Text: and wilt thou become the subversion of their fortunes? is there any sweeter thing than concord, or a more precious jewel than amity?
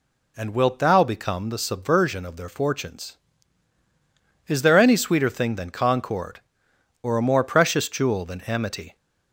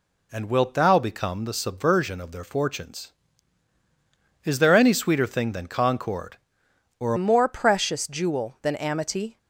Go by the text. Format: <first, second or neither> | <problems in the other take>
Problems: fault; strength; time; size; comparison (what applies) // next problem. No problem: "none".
first | changes voice at "more"; from 7.1 s on; 2.2 s long